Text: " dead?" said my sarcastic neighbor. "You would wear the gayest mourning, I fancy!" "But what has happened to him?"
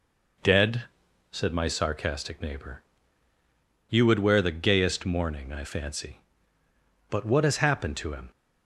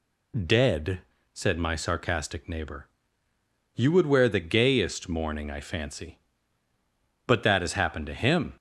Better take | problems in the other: first | says "that" for "what"; at 7.4 s

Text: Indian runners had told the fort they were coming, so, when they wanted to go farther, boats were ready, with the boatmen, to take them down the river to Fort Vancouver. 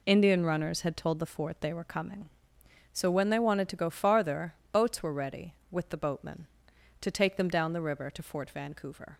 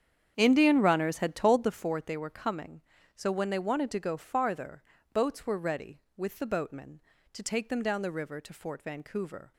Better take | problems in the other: first | starts louder than the rest; strong; until 1.9 s; 8.5 dB

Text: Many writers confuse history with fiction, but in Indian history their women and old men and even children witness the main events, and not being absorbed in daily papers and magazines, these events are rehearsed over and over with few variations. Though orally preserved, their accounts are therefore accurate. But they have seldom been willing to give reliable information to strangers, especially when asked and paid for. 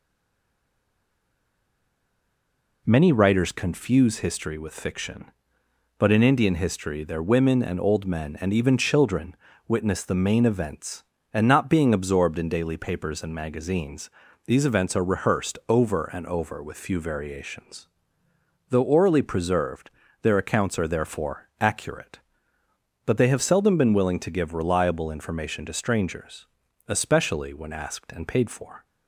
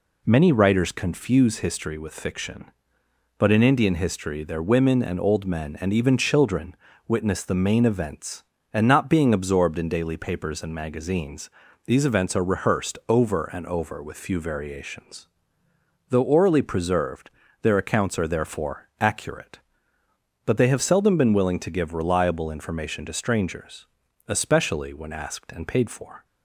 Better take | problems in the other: second | stays silent before the first word; strong; until 2.8 s; 2.8 s long // pauses between "children" and "witness"; slight; at 9.3 s; 0.32 s long; slight in the second

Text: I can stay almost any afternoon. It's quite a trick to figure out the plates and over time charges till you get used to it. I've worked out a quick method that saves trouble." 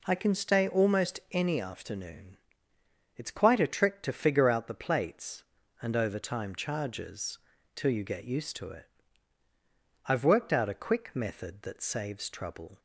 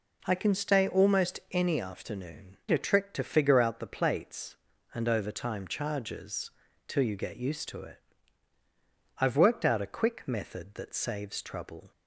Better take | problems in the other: first | skips "It's quite"; at 2.6 s // pauses between "charges" and "till"; at 6.4 s; 0.38 s long; also in the first

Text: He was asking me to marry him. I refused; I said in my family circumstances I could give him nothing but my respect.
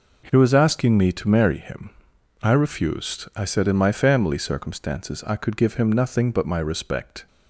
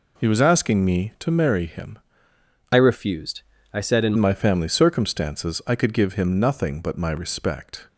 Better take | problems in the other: first | changes voice from "refused" to "in"; from 2.7 to 4.1 s; 1.4 s long

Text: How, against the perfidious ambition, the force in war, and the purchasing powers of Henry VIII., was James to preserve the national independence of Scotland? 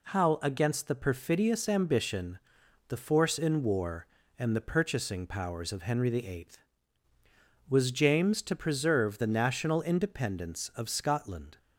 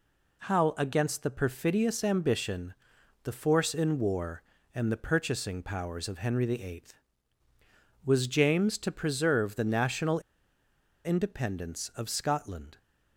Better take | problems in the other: first | pauses between "national" and "independence"; noticeable; at 10.1 s; 0.85 s long

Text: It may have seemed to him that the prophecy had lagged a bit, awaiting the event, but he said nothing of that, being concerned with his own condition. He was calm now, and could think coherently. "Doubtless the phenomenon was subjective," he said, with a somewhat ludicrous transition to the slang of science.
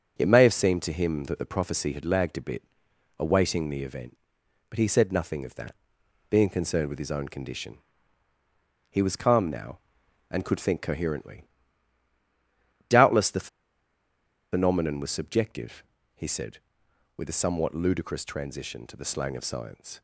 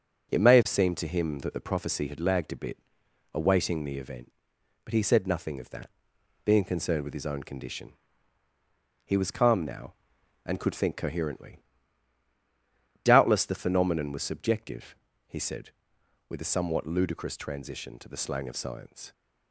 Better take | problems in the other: second | starts louder than the rest; until 1.2 s; 6.5 dB // pauses between "the" and "phenomenon"; at 13.4 s; 1.0 s long

